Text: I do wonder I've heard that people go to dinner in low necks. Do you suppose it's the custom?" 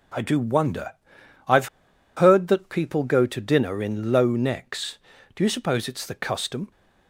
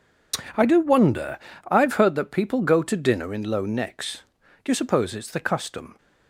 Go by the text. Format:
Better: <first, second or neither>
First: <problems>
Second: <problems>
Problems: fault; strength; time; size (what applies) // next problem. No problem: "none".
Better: second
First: pauses between "wonder" and "I've"; noticeable; at 0.9 s; 0.56 s long // pauses between "I've" and "heard"; noticeable; at 1.6 s; 0.48 s long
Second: pauses between "wonder" and "I've"; slight; at 1.3 s; 0.30 s long